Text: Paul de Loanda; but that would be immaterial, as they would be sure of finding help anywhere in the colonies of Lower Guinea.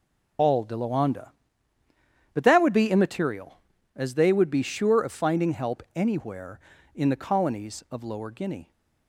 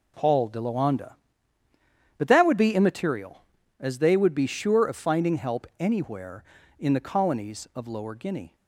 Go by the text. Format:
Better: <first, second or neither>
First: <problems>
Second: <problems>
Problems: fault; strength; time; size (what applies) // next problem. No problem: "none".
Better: second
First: loses the start of "Paul"; at 0.3 s; 85 ms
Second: none